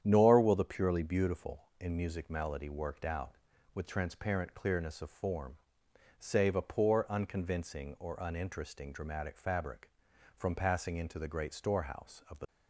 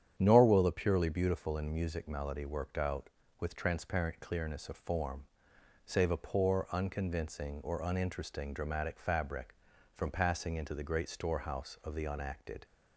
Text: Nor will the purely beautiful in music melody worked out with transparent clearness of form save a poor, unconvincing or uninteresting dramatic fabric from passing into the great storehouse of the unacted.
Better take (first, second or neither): second